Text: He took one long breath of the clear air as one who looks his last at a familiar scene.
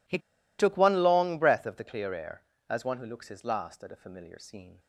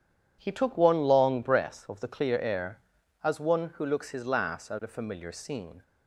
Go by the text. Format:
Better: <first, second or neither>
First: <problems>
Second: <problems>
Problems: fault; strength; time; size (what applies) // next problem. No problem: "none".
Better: second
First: pauses between "He" and "took"; at 0.1 s; 0.40 s long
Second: none